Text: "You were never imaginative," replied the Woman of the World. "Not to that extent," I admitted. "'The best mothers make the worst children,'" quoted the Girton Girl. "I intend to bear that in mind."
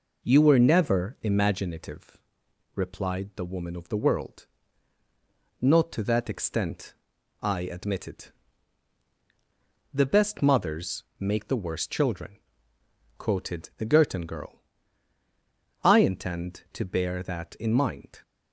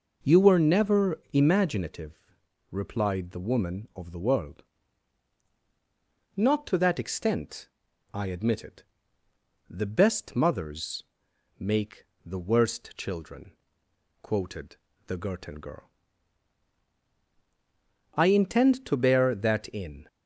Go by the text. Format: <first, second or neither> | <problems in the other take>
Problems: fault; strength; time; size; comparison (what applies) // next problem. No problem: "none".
first | pauses between "mothers" and "make"; noticeable; at 11.0 s; 0.54 s long; slight in the first // pauses between "make" and "the"; slight; at 12.0 s; 0.20 s long // pauses between "quoted" and "the"; slight; at 14.7 s; 0.30 s long // stops before "mind"; at 20.0 s